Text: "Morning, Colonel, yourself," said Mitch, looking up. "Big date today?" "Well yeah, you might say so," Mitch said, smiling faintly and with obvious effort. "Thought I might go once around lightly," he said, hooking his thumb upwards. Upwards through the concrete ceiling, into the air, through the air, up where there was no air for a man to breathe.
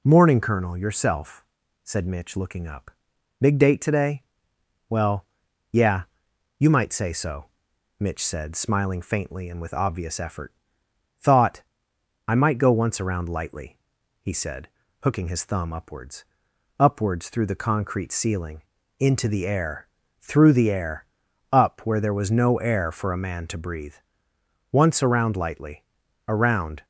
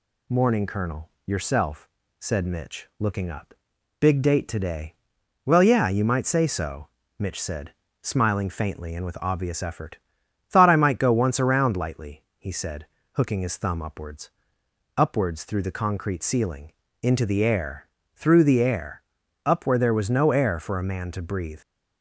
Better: second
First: pauses between "Well" and "yeah"; at 5.2 s; 0.44 s long // pauses between "Thought" and "I"; noticeable; at 11.6 s; 0.66 s long // goes on to say "Once around lightly Around"; strong; from 24.7 s on; 2.1 s long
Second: none

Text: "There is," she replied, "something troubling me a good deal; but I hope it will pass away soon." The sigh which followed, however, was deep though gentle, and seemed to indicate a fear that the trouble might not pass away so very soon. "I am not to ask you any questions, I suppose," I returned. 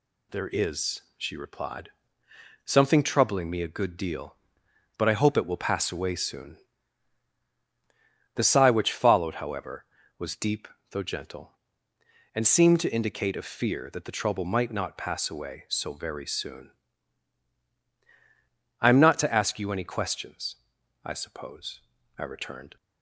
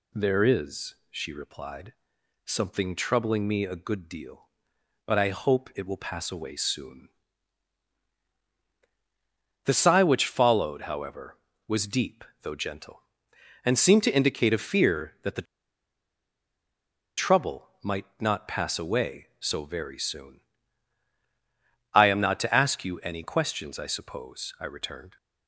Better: first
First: pauses between "deep" and "though"; slight; at 10.6 s; 0.24 s long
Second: pauses between "deep" and "though"; slight; at 12.2 s; 0.18 s long // pauses between "the" and "trouble"; strong; at 15.4 s; 1.7 s long

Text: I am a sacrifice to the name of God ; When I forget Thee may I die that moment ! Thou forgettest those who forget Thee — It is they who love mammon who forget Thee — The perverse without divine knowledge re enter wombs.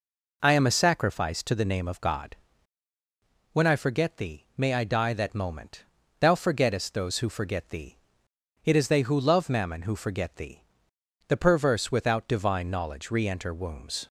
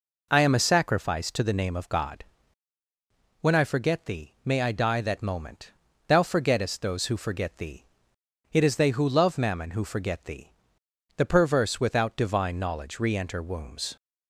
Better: neither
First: none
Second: none

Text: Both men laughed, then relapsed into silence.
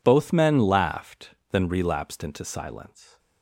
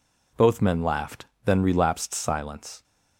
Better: first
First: none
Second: skips "into"; at 2.1 s

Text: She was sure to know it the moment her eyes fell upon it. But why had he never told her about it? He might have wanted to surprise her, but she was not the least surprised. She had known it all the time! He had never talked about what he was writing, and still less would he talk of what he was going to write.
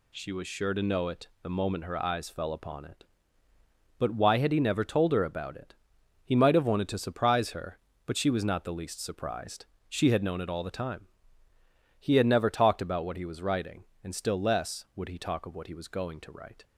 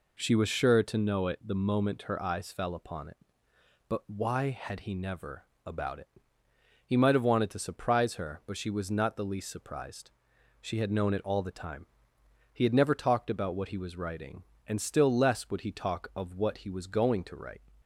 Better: first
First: none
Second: skips "told her"; at 5.5 s

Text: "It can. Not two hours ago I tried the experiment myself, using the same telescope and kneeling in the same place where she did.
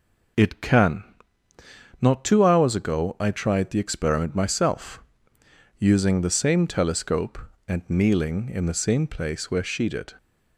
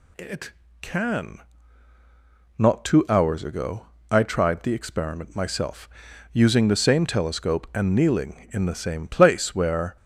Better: first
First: none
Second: pauses between "ago" and "I"; slight; at 3.8 s; 0.26 s long // stops before "she did"; at 9.9 s

